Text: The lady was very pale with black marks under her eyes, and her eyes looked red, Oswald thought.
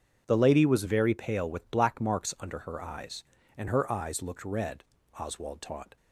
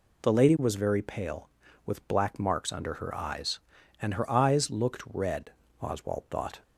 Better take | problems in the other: second | says "taught" for "thought"; at 5.5 s

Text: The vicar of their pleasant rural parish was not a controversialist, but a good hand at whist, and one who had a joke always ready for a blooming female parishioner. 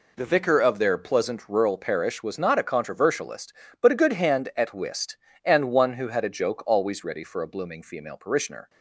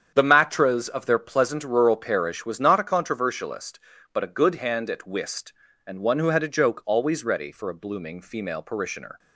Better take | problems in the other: first | starts louder than the rest; strong; until 1.1 s; 8 dB // says "matras" for "vicar"; at 0.2 s

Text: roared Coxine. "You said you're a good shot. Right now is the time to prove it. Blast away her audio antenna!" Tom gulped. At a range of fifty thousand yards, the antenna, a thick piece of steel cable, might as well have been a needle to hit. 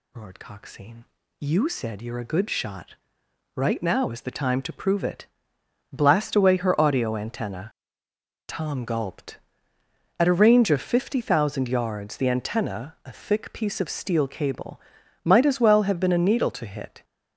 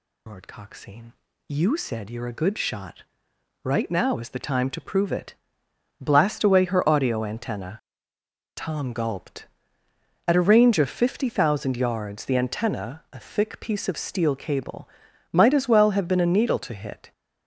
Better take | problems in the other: first | loses the start of "roared"; at 0.2 s; 35 ms

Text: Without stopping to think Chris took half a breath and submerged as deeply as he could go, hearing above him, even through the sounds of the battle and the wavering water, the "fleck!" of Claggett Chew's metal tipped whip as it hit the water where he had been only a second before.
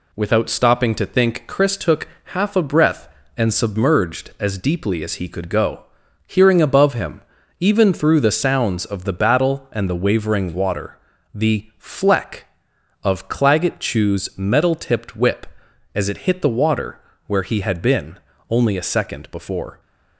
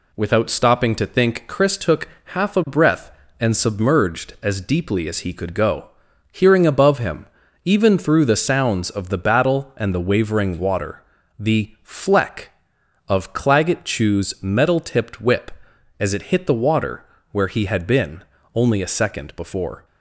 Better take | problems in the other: neither | pauses between "took" and "half"; slight; the same in both // pauses between "water" and "where"; slight; the same in both // pauses between "been" and "only"; slight; the same in both

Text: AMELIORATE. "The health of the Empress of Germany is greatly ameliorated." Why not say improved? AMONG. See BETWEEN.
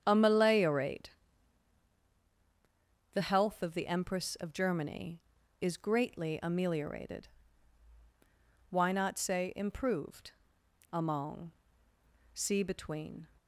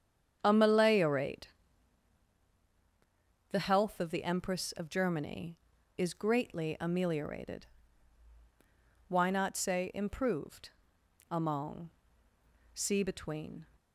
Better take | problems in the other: neither | starts louder than the rest; strong; the same in both

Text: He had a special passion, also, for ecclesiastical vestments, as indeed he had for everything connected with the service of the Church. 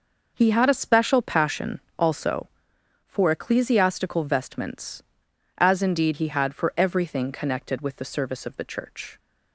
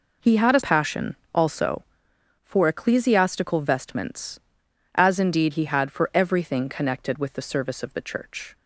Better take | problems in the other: first | skips "special"; at 0.6 s

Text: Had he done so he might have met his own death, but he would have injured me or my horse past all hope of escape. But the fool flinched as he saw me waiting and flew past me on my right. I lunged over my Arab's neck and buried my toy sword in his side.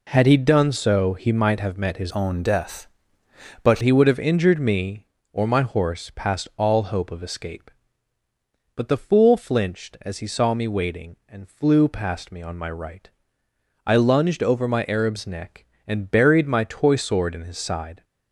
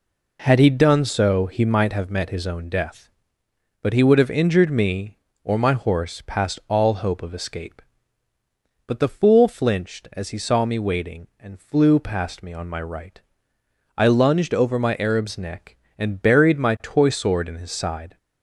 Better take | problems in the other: second | changes voice from "own" to "but"; from 2.0 to 3.7 s; 1.7 s long

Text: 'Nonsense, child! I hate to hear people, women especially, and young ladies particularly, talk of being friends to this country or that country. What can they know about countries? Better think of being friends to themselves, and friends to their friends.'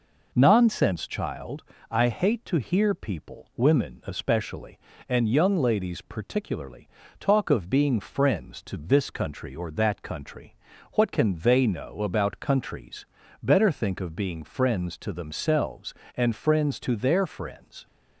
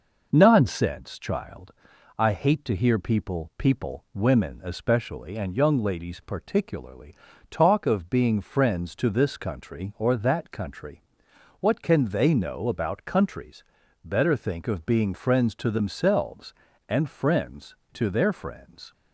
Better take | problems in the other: first | says "people" twice; at 3.5 s

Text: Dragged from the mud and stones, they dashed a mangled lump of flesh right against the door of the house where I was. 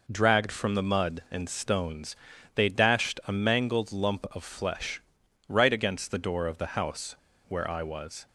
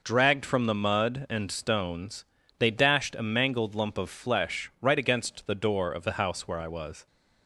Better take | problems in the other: second | pauses between "flesh" and "right"; noticeable; at 5.0 s; 0.48 s long // pauses between "house" and "where"; slight; at 7.1 s; 0.33 s long

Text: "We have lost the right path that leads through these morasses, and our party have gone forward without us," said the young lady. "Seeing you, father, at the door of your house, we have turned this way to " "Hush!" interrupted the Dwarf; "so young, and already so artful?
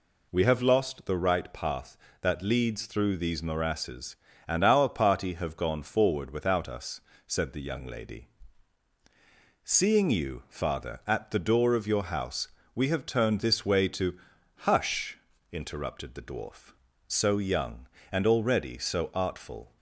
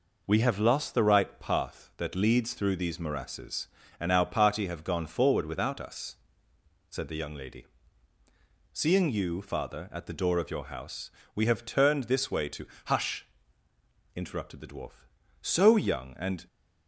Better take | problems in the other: first | stops before "already so artful"; at 16.4 s

